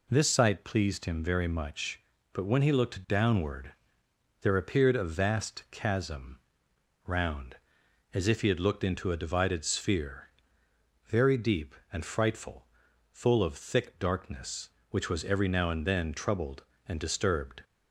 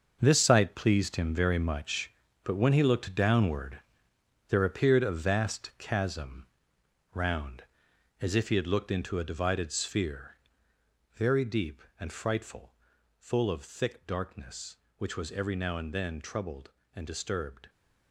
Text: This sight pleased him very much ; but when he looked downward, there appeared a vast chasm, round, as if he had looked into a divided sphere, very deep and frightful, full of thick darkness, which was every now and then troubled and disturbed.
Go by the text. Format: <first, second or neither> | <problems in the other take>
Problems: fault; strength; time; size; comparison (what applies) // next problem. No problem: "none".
first | gets quieter; strong; throughout; 11 dB